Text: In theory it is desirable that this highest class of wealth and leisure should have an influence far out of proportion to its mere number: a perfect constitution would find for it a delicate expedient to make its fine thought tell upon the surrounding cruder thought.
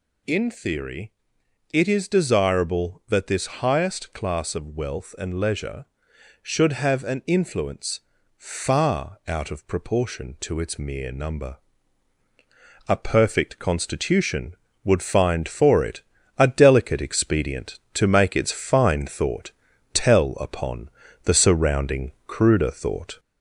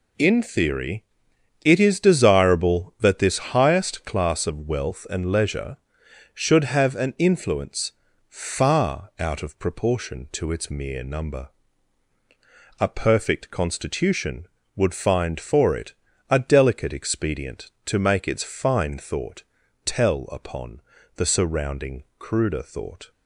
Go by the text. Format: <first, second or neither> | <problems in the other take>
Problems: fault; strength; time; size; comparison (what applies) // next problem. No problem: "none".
second | gets louder; slight; throughout; 2 dB // pauses between "theory" and "it"; noticeable; at 1.1 s; 0.62 s long; noticeable in the second // pauses between "influence" and "far"; at 7.9 s; 0.38 s long; also in the second // pauses between "it" and "a"; slight; at 16.0 s; 0.34 s long; slight in the second // pauses between "thought" and "tell"; at 19.5 s; 0.40 s long; also in the second // pauses between "upon" and "the"; slight; at 20.8 s; 0.36 s long; slight in the second